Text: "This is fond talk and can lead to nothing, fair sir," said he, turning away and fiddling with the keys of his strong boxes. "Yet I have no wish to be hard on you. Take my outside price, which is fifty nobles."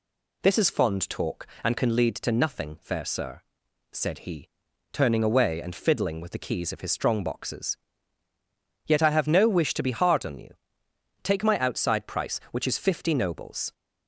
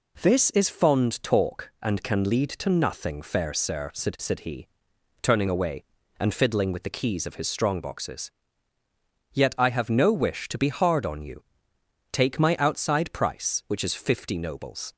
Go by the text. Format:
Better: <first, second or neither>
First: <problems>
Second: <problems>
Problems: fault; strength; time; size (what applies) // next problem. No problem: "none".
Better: first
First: none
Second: says "said" twice; at 4.1 s